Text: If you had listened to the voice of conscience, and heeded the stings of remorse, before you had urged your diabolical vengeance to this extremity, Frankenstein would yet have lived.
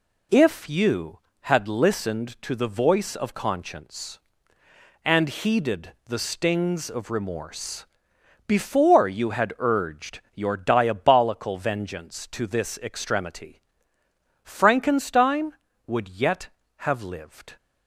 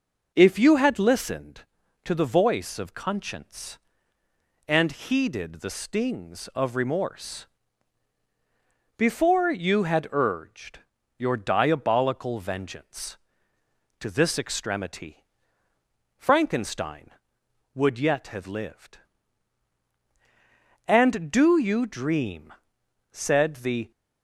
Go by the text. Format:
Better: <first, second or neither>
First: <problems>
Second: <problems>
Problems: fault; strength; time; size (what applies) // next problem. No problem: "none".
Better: first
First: pauses between "urged" and "your"; slight; at 10.2 s; 0.16 s long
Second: pauses between "urged" and "your"; at 10.7 s; 0.40 s long // goes on to say "And do you dream said the"; strong; from 20.8 s on; 3.0 s long